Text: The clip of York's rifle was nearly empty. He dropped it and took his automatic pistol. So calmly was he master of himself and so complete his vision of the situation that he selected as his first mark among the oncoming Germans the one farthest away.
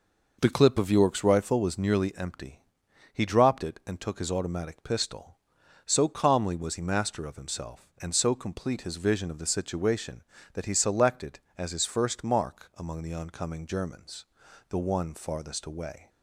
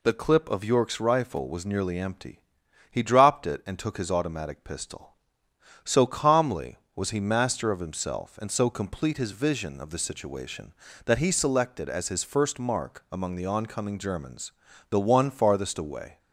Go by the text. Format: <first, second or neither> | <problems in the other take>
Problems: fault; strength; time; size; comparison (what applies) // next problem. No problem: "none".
second | starts louder than the rest; noticeable; until 1.9 s; 5.5 dB // pauses between "Germans" and "the"; at 14.2 s; 0.42 s long; slight in the second